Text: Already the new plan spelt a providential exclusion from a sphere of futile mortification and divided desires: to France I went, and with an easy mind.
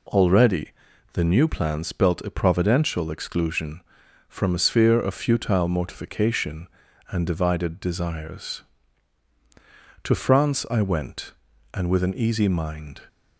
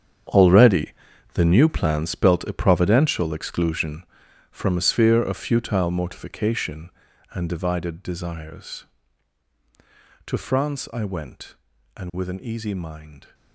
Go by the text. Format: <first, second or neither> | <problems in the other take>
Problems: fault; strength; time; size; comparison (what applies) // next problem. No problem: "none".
first | gets quieter; strong; throughout; 13.5 dB // pauses between "Already" and "the"; at 0.9 s; 0.42 s long; also in the first